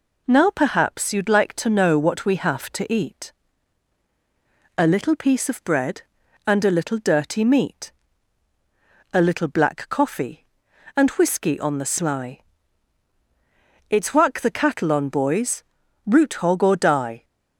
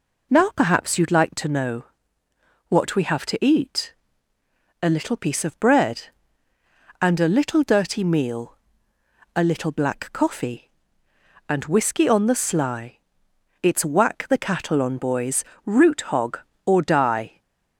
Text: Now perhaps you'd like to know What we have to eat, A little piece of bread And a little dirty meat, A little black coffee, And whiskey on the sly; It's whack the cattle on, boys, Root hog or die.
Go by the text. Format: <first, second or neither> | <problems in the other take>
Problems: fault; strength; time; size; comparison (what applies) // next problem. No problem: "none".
first | pauses between "know" and "What"; noticeable; at 1.8 s; 0.84 s long // says "meal" for "meat"; at 8.0 s // stays silent after the last word; slight; from 17.2 s on; 0.5 s long